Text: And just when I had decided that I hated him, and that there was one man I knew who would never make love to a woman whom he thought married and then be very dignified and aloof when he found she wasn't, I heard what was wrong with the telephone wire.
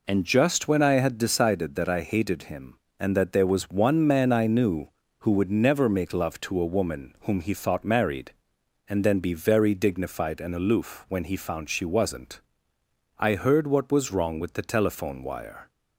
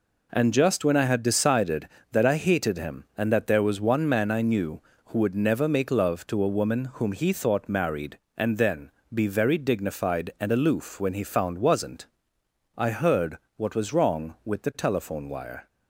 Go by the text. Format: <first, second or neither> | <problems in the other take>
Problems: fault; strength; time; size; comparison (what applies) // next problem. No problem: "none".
first | pauses between "then" and "be"; slight; at 8.9 s; 0.20 s long // skips "she"; at 11.5 s // pauses between "heard" and "what"; slight; at 13.3 s; 0.18 s long